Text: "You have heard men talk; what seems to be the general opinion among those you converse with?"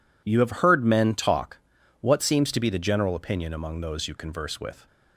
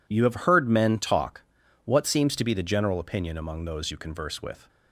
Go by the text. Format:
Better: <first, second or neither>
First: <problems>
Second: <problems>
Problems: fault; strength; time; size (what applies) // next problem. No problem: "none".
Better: neither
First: none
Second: none